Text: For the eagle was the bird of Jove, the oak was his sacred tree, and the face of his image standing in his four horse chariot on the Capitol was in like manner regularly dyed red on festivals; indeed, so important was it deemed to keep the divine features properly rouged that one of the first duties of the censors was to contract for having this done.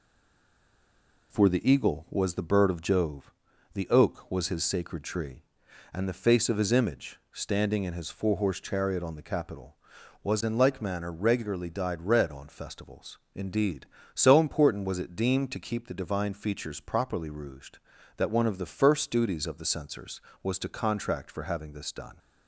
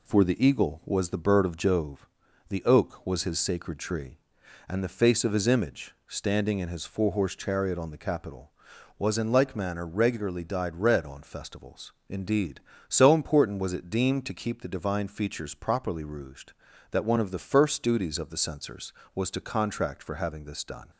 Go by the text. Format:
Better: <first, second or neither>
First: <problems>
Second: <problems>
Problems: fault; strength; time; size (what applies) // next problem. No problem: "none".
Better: second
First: stays silent before the first word; noticeable; until 1.3 s; 1.3 s long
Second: none